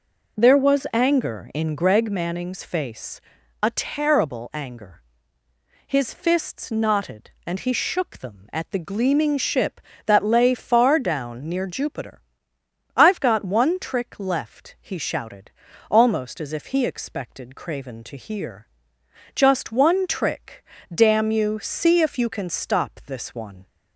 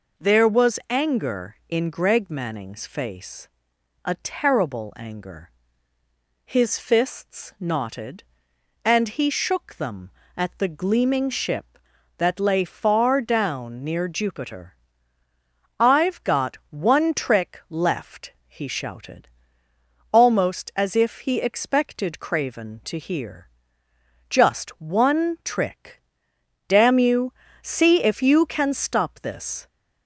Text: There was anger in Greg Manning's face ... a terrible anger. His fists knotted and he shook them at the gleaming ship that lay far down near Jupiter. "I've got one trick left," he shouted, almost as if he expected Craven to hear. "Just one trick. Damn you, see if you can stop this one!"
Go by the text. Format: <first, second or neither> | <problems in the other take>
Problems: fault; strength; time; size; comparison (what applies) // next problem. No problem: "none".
first | stops before "one"; at 29.6 s